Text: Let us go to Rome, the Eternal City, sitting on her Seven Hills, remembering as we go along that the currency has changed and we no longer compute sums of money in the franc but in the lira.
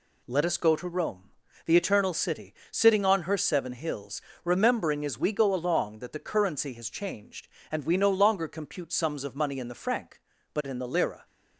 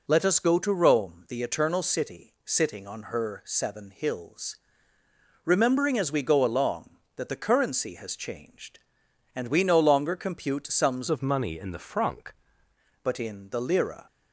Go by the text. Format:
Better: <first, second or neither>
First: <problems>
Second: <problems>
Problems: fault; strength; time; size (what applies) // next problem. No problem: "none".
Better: first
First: none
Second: changes voice from "of" to "franc"; from 11.0 to 12.3 s; 1.3 s long